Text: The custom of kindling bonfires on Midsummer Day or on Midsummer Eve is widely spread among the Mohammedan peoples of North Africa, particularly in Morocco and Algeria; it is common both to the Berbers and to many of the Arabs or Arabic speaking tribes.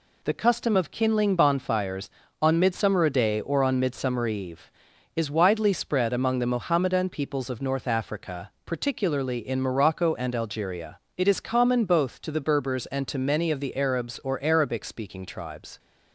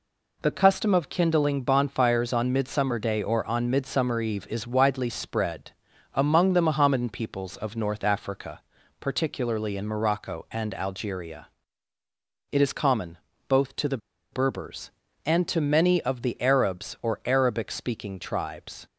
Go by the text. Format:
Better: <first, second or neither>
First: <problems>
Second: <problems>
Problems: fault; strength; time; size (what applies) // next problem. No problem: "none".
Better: first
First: none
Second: pauses between "spread" and "among"; at 5.7 s; 0.42 s long // pauses between "common" and "both"; slight; at 13.1 s; 0.30 s long // pauses between "the" and "Berbers"; slight; at 13.9 s; 0.33 s long